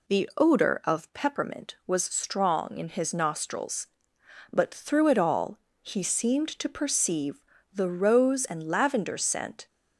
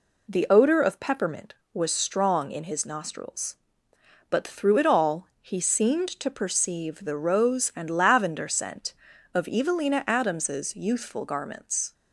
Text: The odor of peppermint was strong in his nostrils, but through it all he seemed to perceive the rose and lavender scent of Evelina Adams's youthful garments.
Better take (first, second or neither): second